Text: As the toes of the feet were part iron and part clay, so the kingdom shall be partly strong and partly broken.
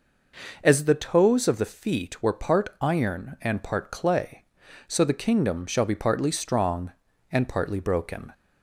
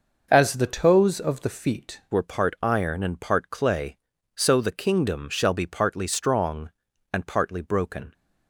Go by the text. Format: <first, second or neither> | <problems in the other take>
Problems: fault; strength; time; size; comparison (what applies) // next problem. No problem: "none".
first | changes voice at "were"; from 2.1 s on; 6.0 s long